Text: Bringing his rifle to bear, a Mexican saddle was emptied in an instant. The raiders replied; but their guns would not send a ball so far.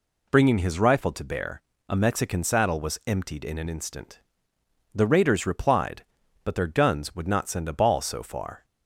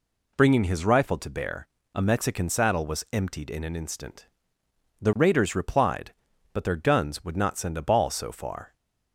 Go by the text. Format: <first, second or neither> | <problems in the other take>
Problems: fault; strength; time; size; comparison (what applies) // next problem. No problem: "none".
neither | none